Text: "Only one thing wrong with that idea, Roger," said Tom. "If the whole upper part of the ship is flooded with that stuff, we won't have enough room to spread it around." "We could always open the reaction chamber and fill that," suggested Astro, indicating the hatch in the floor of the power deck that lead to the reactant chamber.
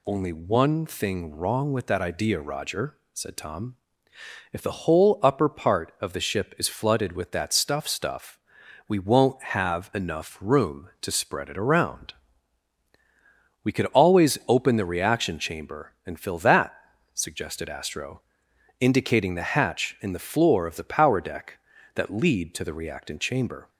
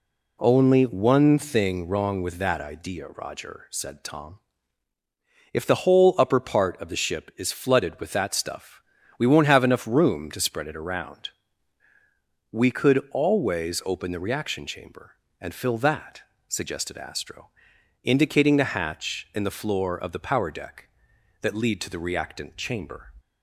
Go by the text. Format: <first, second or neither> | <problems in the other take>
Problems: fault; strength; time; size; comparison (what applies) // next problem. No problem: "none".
second | says "stuff" twice; at 7.8 s